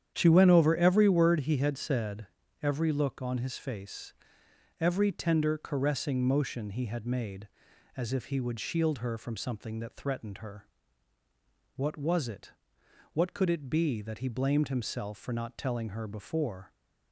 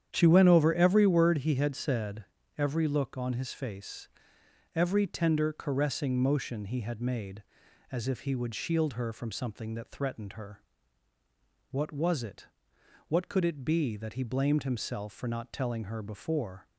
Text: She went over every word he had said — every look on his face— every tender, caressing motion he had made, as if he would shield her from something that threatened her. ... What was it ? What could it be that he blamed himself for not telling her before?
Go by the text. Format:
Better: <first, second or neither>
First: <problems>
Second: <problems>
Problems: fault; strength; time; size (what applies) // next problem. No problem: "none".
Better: neither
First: starts louder than the rest; strong; until 1.1 s; 9 dB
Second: starts louder than the rest; strong; until 1.1 s; 9 dB